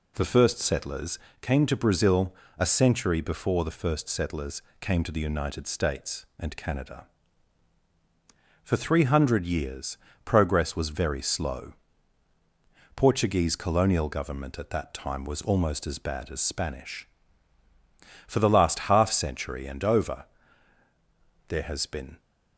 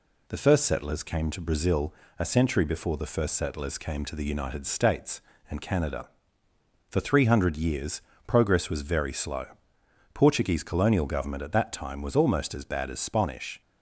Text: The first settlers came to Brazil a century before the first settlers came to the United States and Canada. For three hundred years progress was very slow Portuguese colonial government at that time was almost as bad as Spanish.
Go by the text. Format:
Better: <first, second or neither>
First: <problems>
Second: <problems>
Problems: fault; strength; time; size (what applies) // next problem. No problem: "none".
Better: second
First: pauses between "settlers" and "came"; slight; at 1.1 s; 0.22 s long // pauses between "Brazil" and "a"; slight; at 2.3 s; 0.24 s long // pauses between "settlers" and "came"; slight; at 4.6 s; 0.16 s long // pauses between "years" and "progress"; slight; at 9.9 s; 0.28 s long // pauses between "slow" and "Portuguese"; at 11.7 s; 1.2 s long // goes on to say "For the last half century and over there has been"; strong; from 18.2 s on; 3.9 s long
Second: pauses between "Brazil" and "a"; slight; at 1.9 s; 0.26 s long // pauses between "years" and "progress"; slight; at 8.0 s; 0.24 s long // pauses between "slow" and "Portuguese"; noticeable; at 9.4 s; 0.70 s long